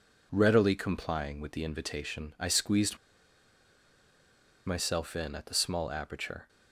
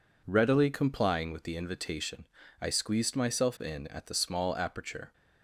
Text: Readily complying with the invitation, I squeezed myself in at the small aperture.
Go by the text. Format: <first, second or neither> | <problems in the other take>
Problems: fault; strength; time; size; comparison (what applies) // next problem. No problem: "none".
second | pauses between "squeezed" and "myself"; strong; at 2.9 s; 1.6 s long